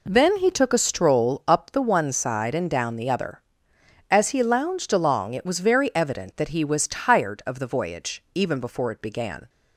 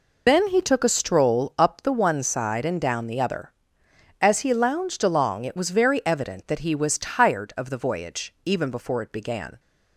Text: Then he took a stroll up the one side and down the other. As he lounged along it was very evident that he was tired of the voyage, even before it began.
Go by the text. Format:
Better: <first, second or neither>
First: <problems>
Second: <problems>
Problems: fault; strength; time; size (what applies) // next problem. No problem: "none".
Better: first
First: none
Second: loses the start of "Then"; at 0.2 s; 100 ms